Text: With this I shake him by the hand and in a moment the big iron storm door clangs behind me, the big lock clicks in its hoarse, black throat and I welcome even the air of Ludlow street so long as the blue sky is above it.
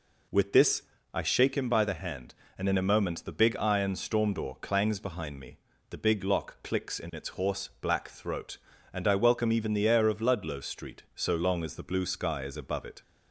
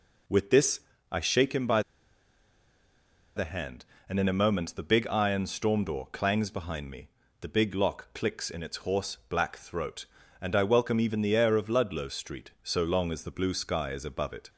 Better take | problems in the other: first | pauses between "this" and "I"; slight; at 0.7 s; 0.32 s long; slight in the first // pauses between "by" and "the"; strong; at 1.8 s; 1.5 s long

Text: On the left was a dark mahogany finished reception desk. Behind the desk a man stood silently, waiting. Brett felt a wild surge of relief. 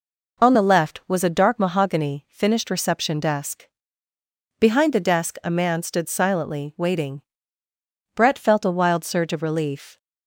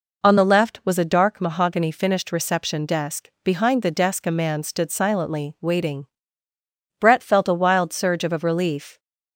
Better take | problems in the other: first | says "of" twice; at 8.3 s

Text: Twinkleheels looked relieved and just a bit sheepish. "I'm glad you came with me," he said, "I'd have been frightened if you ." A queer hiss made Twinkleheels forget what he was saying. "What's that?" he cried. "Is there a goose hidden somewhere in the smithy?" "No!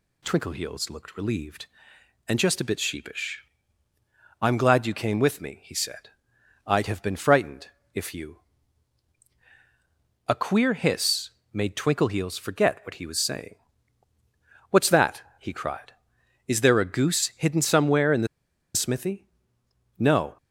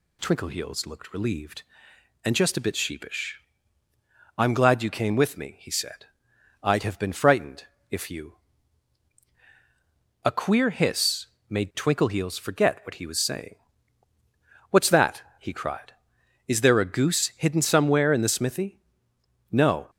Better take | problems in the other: second | pauses between "frightened" and "if"; slight; at 7.6 s; 0.26 s long; slight in the second // pauses between "hiss" and "made"; slight; at 11.2 s; 0.22 s long; slight in the second // pauses between "the" and "smithy"; noticeable; at 18.2 s; 0.47 s long

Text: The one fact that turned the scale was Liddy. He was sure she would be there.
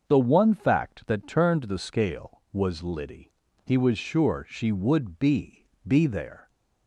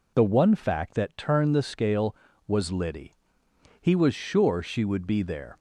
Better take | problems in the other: second | starts louder than the rest; until 1.1 s; 6.5 dB // says "be" twice; at 5.8 s

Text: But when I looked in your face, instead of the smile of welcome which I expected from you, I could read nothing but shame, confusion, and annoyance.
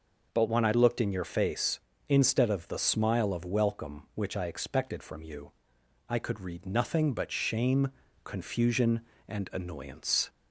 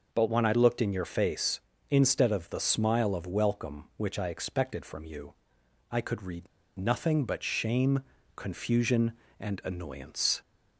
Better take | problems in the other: first | pauses between "read" and "nothing"; slight; at 6.4 s; 0.31 s long

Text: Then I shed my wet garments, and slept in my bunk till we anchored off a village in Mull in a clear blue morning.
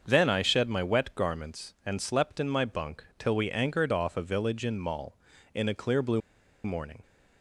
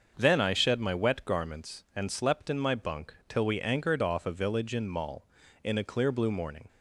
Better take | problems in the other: second | starts louder than the rest; until 1.0 s; 6.5 dB; also in the second // pauses between "bunk" and "till"; slight; at 3.0 s; 0.16 s long; slight in the second // pauses between "blue" and "morning"; at 6.2 s; 0.45 s long

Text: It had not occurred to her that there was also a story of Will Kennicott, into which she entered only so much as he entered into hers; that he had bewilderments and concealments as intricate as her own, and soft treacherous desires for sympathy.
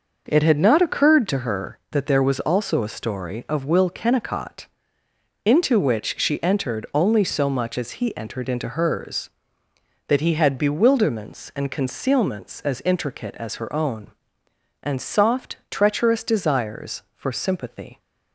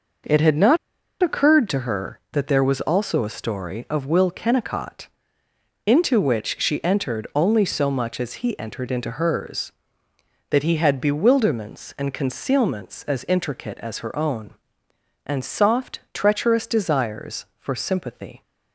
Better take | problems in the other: first | pauses between "not" and "occurred"; noticeable; at 0.7 s; 0.46 s long

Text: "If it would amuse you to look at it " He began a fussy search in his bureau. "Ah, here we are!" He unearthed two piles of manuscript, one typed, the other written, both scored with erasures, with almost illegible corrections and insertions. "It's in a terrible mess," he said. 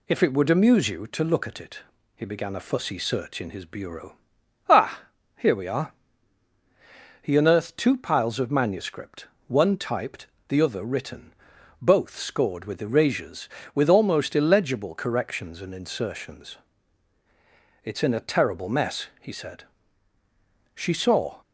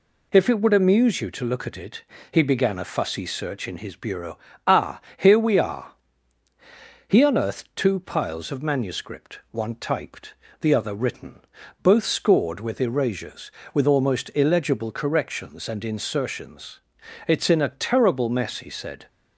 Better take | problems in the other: second | goes on to say "She saw"; noticeable; from 20.7 s on; 0.66 s long

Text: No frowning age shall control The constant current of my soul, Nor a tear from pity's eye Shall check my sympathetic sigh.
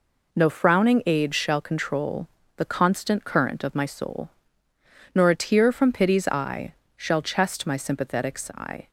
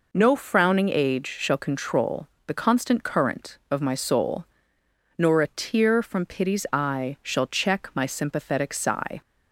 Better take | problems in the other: second | pauses between "control" and "The"; slight; at 2.2 s; 0.26 s long; slight in the second // pauses between "eye" and "Shall"; slight; at 6.7 s; 0.22 s long // says "chest" for "check"; at 7.2 s

